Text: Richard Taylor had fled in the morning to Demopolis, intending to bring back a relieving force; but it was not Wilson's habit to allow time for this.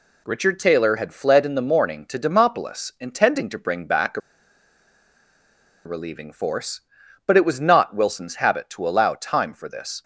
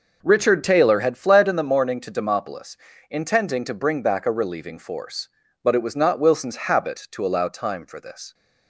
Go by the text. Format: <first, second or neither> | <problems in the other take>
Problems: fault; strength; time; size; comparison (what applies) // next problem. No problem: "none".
second | pauses between "a" and "relieving"; strong; at 4.2 s; 1.6 s long